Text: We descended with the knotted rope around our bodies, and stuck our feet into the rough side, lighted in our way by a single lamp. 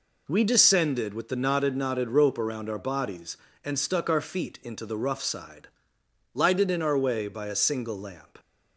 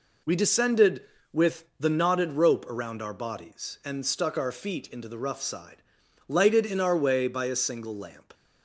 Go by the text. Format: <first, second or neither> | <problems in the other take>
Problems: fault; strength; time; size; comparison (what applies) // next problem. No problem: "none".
second | says "knotted" twice; at 1.7 s